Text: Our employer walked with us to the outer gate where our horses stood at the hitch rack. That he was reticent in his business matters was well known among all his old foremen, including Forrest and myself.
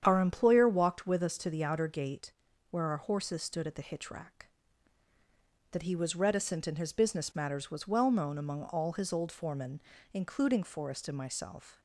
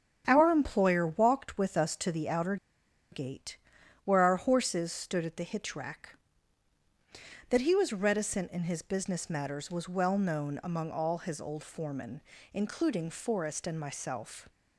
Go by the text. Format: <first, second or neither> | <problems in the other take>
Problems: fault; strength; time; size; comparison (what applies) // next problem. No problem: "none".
first | starts louder than the rest; strong; until 1.2 s; 8.5 dB; strong in the first // pauses between "outer" and "gate"; noticeable; at 2.5 s; 0.56 s long // pauses between "gate" and "where"; noticeable; at 3.5 s; 0.48 s long; also in the first